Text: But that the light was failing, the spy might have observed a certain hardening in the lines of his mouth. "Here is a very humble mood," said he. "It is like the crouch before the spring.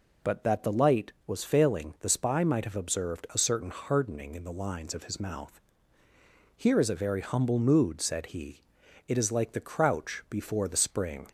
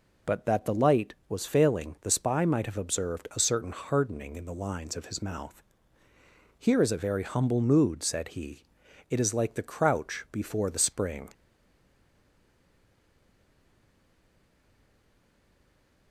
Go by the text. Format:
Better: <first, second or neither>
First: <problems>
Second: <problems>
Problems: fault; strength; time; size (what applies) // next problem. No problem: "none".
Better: first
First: none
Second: stays silent after the last word; strong; from 11.3 s on; 4.8 s long